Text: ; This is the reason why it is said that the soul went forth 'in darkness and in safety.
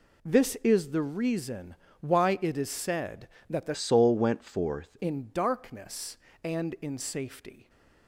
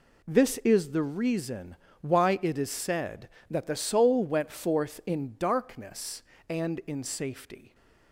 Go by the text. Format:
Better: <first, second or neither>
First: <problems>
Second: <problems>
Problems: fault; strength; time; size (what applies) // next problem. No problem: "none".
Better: second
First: pauses between "reason" and "why"; slight; at 1.7 s; 0.26 s long // changes voice from "soul" to "forth"; from 3.7 to 4.9 s; 1.2 s long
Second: pauses between "reason" and "why"; slight; at 1.7 s; 0.26 s long